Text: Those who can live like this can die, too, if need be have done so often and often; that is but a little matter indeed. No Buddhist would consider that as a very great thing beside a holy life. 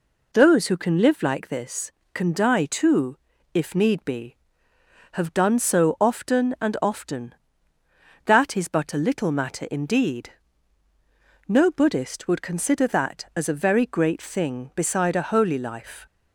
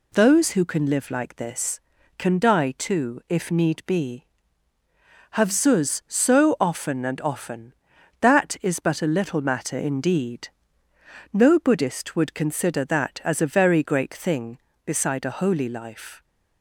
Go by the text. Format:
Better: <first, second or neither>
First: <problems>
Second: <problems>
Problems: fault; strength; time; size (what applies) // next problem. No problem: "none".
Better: first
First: none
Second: says "zuz" for "done"; at 5.5 s